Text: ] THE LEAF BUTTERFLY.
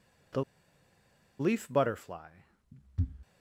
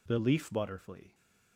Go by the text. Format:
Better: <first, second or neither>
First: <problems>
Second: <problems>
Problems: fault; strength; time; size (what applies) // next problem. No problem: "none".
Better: second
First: pauses between "THE" and "LEAF"; noticeable; at 0.4 s; 0.97 s long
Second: none